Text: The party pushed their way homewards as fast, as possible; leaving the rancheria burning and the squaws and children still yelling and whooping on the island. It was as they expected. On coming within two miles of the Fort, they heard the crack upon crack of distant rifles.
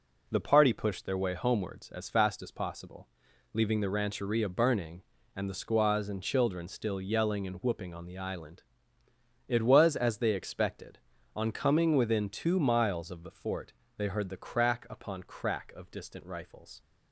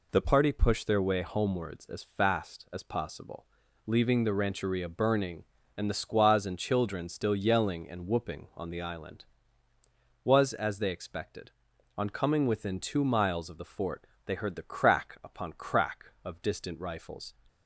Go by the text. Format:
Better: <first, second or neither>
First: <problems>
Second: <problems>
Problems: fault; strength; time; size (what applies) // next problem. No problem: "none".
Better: first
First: none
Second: skips "It"; at 9.7 s